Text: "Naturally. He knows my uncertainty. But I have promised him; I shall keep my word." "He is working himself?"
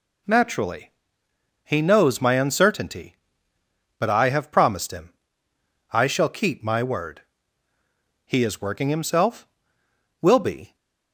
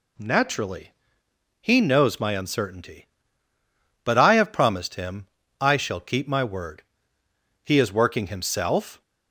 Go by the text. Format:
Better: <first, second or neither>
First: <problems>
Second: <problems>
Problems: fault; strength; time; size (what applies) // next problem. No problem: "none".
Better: second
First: goes on to say "Will be"; from 10.2 s on; 0.54 s long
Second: none